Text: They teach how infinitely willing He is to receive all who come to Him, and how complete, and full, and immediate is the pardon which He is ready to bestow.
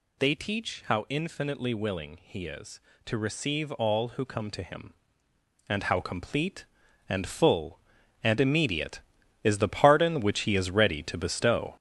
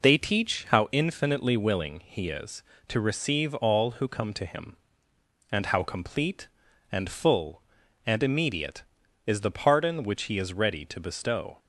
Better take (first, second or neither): second